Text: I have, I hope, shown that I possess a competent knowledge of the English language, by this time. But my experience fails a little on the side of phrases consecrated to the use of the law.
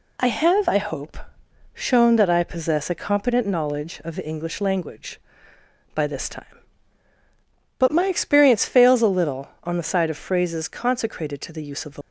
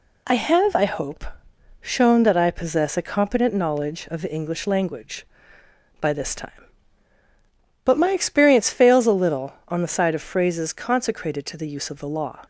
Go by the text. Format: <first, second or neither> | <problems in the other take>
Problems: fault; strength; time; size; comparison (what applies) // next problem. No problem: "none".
second | stops before "law"; at 12.0 s